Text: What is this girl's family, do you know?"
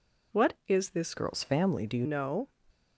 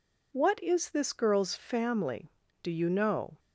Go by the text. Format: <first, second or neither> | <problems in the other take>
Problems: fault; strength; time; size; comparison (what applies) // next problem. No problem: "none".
second | changes voice from "girl's" to "you"; from 1.1 to 2.0 s; 0.9 s long